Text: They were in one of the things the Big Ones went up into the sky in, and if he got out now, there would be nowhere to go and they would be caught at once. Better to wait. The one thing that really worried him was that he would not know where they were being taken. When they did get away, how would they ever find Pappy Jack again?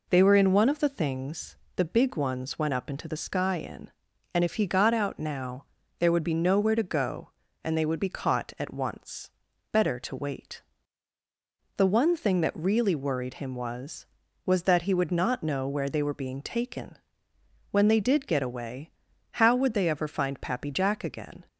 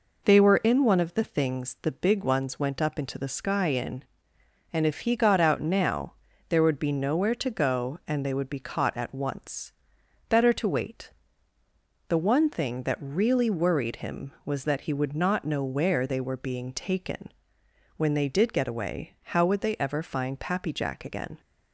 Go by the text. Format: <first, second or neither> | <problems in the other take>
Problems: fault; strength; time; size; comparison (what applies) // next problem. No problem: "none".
second | pauses between "things" and "the"; slight; at 1.5 s; 0.20 s long // says "was" twice; at 14.4 s